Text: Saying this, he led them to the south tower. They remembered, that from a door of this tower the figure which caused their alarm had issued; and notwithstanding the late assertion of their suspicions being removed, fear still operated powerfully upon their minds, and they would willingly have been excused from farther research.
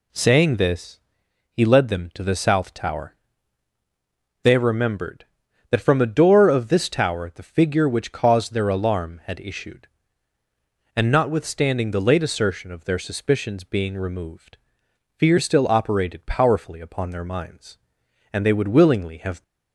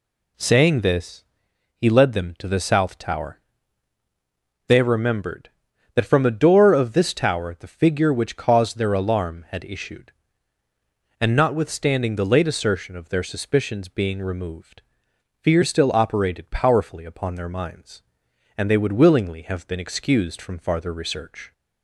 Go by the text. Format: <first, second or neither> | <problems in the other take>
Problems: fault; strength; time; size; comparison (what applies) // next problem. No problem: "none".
second | stops before "been excused from farther research"; at 19.4 s